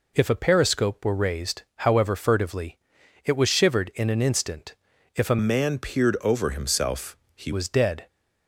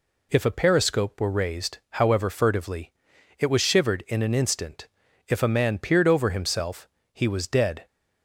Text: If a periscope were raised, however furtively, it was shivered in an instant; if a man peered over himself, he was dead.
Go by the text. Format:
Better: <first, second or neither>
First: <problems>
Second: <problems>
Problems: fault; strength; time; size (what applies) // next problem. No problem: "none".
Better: second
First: changes voice from "man" to "he"; from 5.3 to 7.5 s; 2.2 s long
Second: none